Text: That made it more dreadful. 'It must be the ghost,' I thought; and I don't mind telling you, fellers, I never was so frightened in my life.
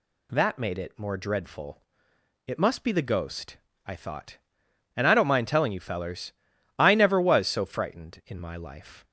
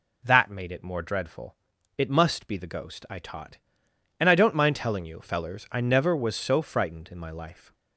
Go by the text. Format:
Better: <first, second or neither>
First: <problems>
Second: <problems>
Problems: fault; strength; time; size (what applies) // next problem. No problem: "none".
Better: first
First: none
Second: says "taught" for "thought"; at 3.1 s